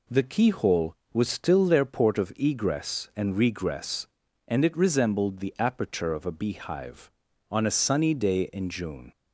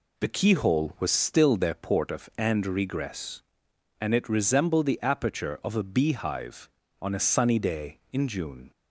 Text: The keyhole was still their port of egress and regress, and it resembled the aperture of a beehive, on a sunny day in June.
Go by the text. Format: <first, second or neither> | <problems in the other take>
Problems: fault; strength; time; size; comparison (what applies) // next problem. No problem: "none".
first | skips "egress"; at 2.3 s